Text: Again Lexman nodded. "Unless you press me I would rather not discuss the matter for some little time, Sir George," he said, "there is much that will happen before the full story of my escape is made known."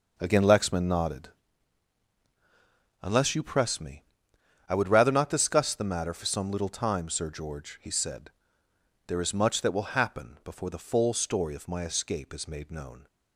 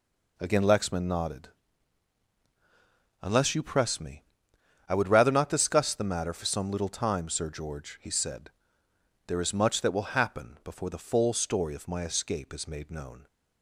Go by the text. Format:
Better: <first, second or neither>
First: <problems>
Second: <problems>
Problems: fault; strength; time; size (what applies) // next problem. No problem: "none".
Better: second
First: starts louder than the rest; noticeable; until 1.5 s; 6 dB // pauses between "me" and "I"; noticeable; at 4.0 s; 0.66 s long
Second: pauses between "me" and "I"; noticeable; at 4.2 s; 0.66 s long